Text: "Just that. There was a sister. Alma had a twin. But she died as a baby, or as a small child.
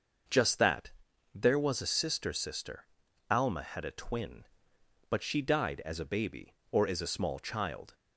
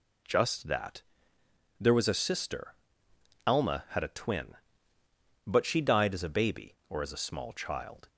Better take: second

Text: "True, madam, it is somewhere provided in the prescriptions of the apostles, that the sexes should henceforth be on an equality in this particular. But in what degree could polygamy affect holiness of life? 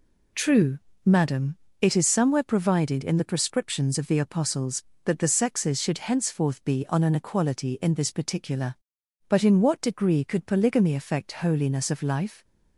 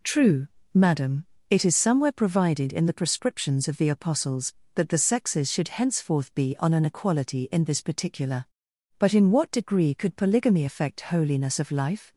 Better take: neither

